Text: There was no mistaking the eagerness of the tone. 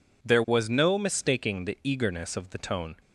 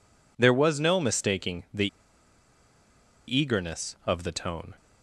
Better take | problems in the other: first | pauses between "the" and "eagerness"; strong; at 1.8 s; 1.4 s long

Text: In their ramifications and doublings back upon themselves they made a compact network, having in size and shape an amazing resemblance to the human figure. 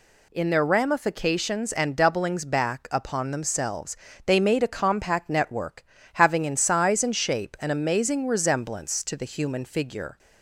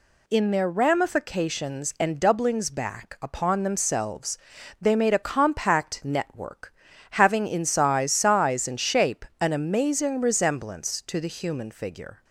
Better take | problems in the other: first | pauses between "themselves" and "they"; at 4.3 s; 0.44 s long; slight in the first // says "size" twice; at 8.1 s // pauses between "shape" and "an"; slight; at 9.2 s; 0.16 s long

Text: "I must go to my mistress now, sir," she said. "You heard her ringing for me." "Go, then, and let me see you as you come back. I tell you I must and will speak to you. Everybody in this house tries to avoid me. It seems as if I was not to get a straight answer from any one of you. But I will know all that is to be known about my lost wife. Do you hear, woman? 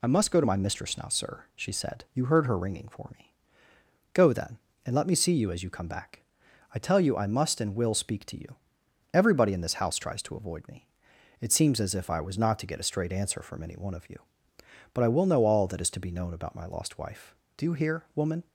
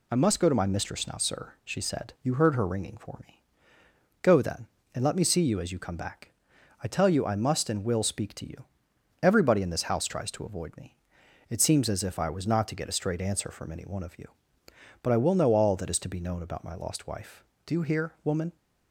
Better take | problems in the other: neither | none

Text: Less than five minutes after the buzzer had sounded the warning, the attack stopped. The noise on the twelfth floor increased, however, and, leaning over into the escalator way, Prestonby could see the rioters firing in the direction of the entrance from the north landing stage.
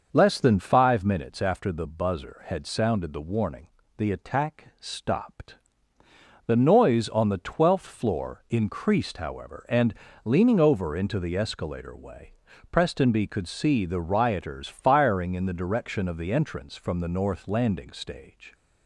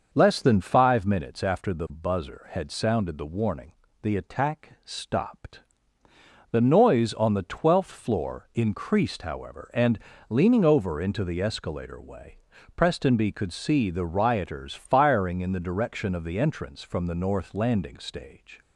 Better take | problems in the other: neither | starts louder than the rest; noticeable; the same in both

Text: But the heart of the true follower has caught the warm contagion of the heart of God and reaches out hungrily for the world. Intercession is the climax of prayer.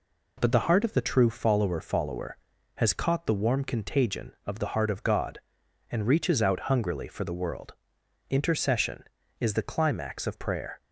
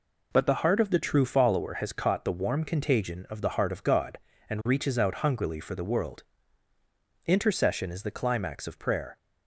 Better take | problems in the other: second | says "follower" twice; at 1.8 s

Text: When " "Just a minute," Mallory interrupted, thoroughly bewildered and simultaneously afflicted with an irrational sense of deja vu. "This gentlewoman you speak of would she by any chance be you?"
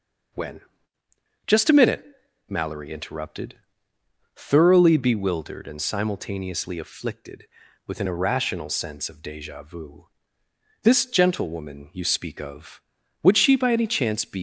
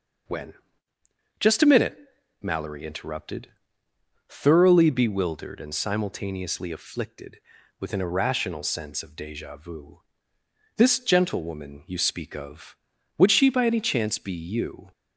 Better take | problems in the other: second | stops before "you"; at 14.3 s

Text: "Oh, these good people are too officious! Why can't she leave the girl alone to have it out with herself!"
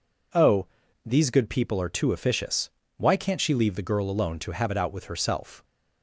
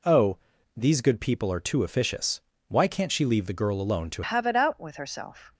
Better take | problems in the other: first | changes voice at "have"; from 4.2 s on; 1.3 s long

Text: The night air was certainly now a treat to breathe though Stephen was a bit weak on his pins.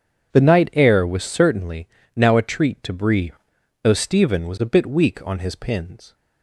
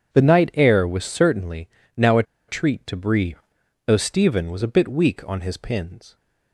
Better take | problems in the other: first | pauses between "certainly" and "now"; slight; at 1.6 s; 0.26 s long; slight in the first // pauses between "a" and "treat"; slight; at 2.2 s; 0.25 s long // pauses between "breathe" and "though"; noticeable; at 3.3 s; 0.48 s long; noticeable in the first

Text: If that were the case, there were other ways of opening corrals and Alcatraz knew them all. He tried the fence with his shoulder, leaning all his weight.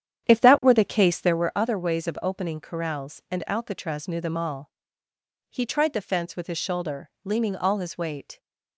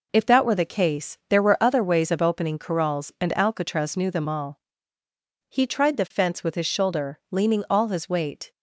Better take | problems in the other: second | starts louder than the rest; strong; until 1.5 s; 9.5 dB

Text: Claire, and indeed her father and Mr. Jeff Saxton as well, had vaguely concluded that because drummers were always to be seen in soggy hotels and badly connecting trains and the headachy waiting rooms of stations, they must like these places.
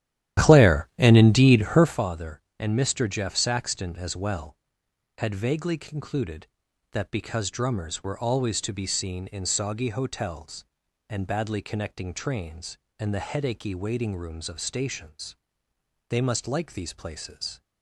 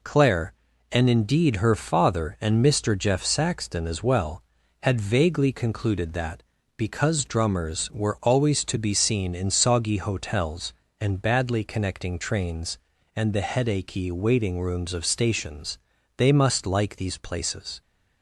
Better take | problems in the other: second | starts louder than the rest; strong; until 2.1 s; 12 dB

